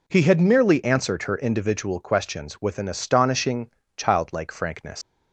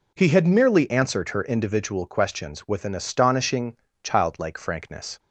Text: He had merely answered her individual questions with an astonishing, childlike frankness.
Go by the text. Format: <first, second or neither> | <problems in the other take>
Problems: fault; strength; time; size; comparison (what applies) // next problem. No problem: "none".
second | leaves "frankness" unfinished; at 5.0 s; 110 ms